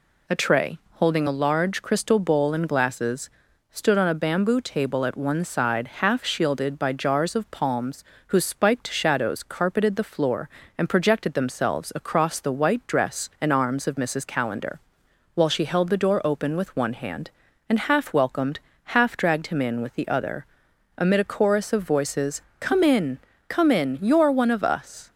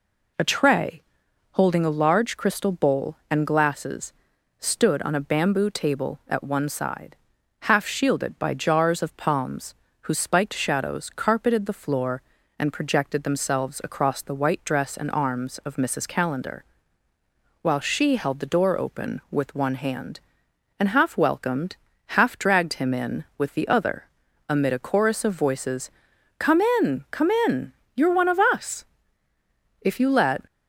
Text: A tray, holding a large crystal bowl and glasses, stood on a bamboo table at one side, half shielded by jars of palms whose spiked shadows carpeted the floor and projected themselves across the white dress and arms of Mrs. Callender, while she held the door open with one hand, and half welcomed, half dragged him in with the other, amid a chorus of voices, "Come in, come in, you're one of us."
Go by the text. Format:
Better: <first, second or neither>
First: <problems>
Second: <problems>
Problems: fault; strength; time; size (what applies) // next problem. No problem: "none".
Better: first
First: pauses between "palms" and "whose"; slight; at 8.0 s; 0.24 s long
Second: pauses between "palms" and "whose"; slight; at 9.7 s; 0.26 s long // goes on to say "If you let"; noticeable; from 29.8 s on; 0.64 s long